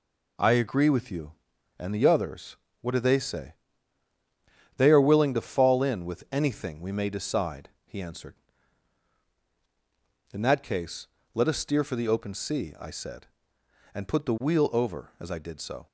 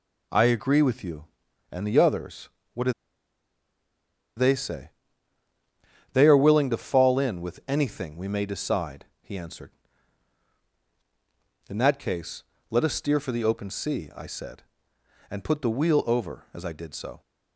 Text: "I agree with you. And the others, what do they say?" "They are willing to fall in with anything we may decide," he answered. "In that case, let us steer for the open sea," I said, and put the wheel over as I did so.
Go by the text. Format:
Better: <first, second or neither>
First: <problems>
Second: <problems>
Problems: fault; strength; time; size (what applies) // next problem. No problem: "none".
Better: first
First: none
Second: pauses between "do" and "they"; strong; at 2.9 s; 1.4 s long